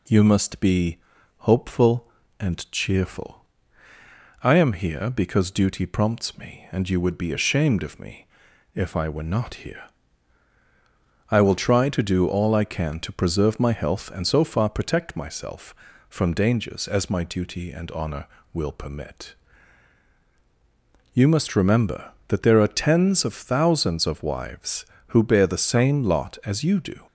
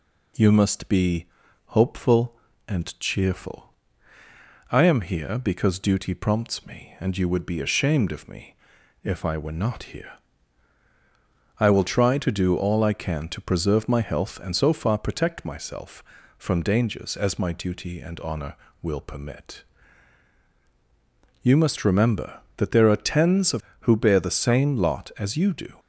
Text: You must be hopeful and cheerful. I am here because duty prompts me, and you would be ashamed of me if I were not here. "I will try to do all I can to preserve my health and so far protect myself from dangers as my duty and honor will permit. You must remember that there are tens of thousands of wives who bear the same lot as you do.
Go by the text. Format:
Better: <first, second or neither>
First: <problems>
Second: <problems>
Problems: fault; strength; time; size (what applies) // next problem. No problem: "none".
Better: first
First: pauses between "be" and "hopeful"; at 0.9 s; 0.40 s long // pauses between "me" and "if"; noticeable; at 8.2 s; 0.50 s long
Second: pauses between "be" and "hopeful"; at 1.2 s; 0.40 s long // pauses between "me" and "if"; noticeable; at 8.5 s; 0.50 s long // skips "thousands of wives"; at 23.7 s